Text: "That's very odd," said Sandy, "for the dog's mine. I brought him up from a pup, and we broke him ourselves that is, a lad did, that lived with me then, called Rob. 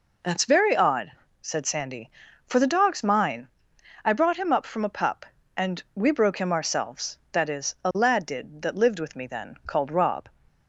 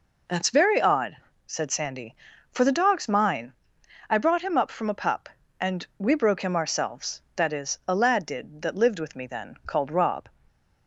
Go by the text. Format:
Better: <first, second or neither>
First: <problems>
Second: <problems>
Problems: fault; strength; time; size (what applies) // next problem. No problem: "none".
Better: neither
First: none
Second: none